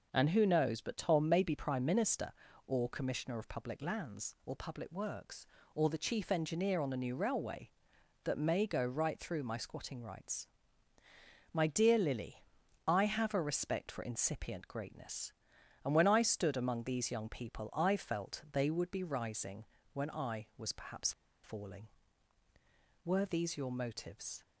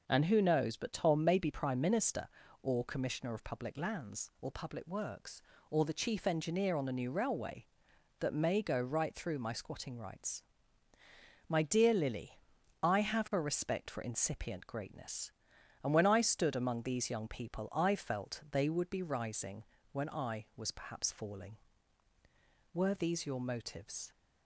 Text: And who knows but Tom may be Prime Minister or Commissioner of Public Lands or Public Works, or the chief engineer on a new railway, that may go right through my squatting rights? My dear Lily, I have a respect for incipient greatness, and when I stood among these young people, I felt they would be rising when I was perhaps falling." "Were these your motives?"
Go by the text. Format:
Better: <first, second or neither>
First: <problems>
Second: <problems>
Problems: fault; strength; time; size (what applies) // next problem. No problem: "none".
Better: second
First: pauses between "rising" and "when"; slight; at 19.6 s; 0.30 s long // pauses between "perhaps" and "falling"; slight; at 21.1 s; 0.31 s long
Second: pauses between "rising" and "when"; slight; at 19.6 s; 0.30 s long